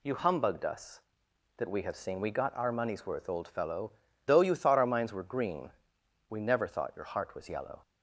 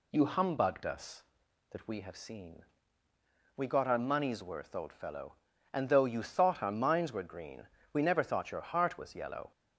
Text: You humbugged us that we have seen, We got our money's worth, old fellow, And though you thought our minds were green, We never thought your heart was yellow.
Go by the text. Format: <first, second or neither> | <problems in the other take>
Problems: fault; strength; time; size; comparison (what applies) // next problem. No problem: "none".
second | skips "And"; at 4.0 s